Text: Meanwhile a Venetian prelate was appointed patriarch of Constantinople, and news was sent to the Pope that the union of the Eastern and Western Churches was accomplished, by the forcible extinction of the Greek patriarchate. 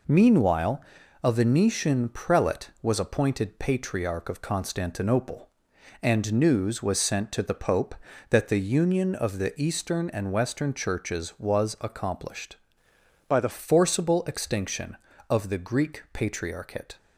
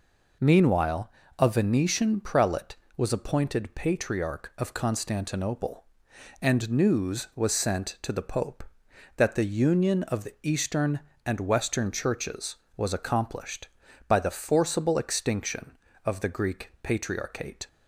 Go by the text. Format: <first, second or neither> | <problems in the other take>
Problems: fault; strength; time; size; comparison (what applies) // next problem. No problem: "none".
second | pauses between "Meanwhile" and "a"; at 0.8 s; 0.42 s long; slight in the second // changes voice from "by" to "the"; from 13.2 to 13.4 s; 0.2 s long